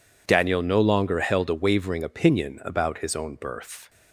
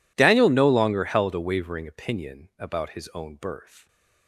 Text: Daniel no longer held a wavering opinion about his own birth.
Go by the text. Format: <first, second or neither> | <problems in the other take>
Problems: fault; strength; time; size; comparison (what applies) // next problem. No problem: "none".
neither | none